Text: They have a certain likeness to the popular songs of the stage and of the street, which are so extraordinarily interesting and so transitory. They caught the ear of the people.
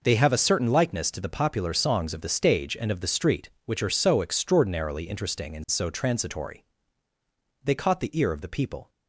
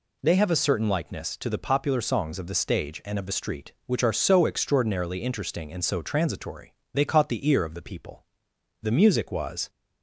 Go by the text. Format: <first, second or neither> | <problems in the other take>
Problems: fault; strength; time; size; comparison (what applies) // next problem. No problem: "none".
first | goes on to say "The music was"; noticeable; from 8.8 s on; 0.88 s long